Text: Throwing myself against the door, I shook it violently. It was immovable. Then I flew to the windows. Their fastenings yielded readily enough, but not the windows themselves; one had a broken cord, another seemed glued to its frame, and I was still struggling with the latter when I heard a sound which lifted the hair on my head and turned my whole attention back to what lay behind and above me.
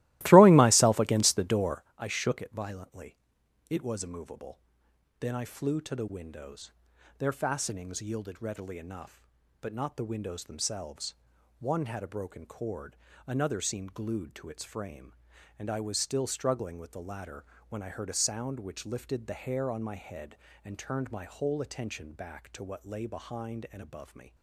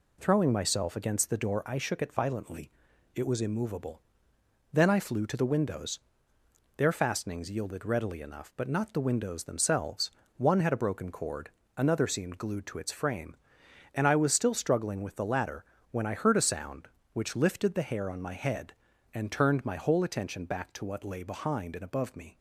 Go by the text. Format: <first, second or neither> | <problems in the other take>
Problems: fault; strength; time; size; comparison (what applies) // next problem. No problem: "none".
second | starts louder than the rest; strong; until 1.9 s; 17.5 dB // pauses between "latter" and "when"; slight; at 17.4 s; 0.24 s long; slight in the second